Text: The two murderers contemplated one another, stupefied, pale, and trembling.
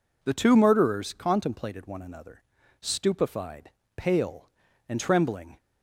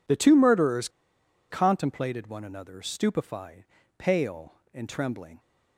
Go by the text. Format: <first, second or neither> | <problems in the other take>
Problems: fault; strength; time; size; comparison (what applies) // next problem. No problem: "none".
first | pauses between "murderers" and "contemplated"; noticeable; at 0.8 s; 0.61 s long